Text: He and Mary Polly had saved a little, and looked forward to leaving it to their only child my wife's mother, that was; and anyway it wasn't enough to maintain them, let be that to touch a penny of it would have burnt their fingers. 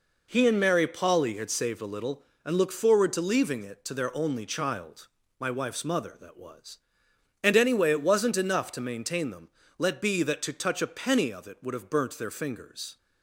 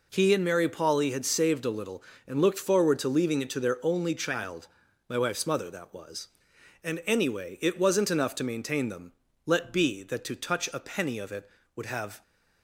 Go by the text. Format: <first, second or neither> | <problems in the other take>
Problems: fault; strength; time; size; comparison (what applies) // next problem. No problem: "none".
first | pauses between "child" and "my"; at 4.6 s; 0.42 s long; slight in the first // stops before "burnt their fingers"; at 12.2 s